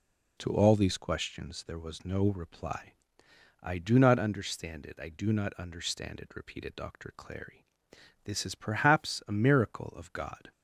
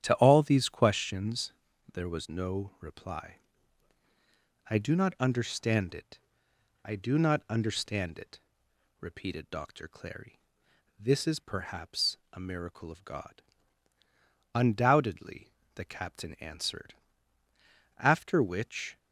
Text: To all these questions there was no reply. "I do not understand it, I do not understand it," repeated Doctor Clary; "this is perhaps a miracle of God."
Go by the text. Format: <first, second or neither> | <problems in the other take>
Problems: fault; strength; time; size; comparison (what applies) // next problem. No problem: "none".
first | starts louder than the rest; strong; until 1.0 s; 10 dB // pauses between "questions" and "there"; at 1.5 s; 0.40 s long // pauses between "perhaps" and "a"; slight; at 12.1 s; 0.16 s long // goes on to say "Undoubtedly the captain answered After which"; strong; from 14.5 s on; 4.4 s long